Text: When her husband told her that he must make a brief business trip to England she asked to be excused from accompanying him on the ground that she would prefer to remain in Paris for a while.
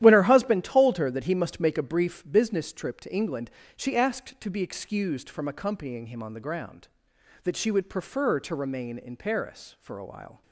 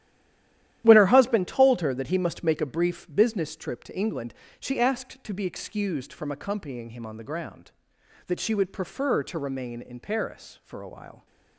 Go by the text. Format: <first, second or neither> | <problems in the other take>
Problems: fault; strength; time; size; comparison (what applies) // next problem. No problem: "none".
first | stays silent before the first word; slight; until 0.8 s; 0.8 s long // starts louder than the rest; strong; until 1.8 s; 12 dB; strong in the first // pauses between "England" and "she"; slight; at 4.3 s; 0.24 s long; slight in the first